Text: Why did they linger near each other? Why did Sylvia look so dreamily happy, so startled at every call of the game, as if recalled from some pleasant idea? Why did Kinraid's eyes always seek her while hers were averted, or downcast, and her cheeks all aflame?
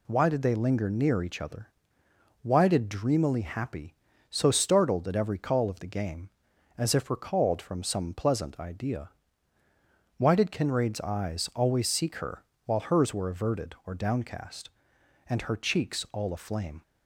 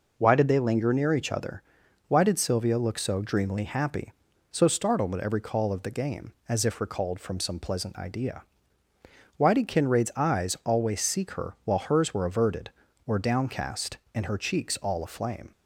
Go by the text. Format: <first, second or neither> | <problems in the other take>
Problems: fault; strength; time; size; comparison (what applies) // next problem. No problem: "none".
second | skips "Sylvia look so"; at 2.8 s // pauses between "her" and "while"; slight; at 12.4 s; 0.22 s long